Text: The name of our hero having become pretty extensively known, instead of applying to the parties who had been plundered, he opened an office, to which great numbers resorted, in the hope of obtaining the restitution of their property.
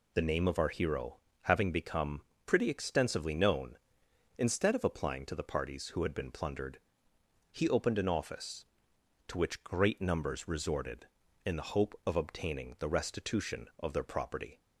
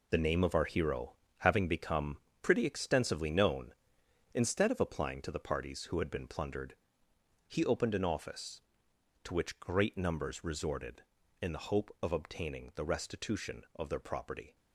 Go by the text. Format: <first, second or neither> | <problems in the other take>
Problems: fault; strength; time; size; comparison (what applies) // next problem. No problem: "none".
first | gets quieter; strong; throughout; 9.5 dB // pauses between "hero" and "having"; slight; at 1.1 s; 0.24 s long; slight in the first // pauses between "become" and "pretty"; slight; at 2.1 s; 0.24 s long; slight in the first